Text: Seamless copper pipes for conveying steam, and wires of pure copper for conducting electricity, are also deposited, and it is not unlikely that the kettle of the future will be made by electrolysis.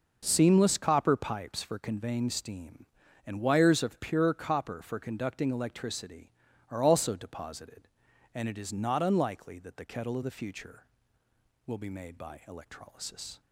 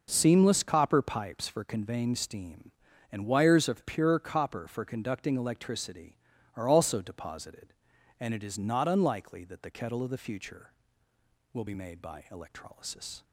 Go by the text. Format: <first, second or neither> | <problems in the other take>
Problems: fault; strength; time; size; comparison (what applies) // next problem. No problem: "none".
neither | none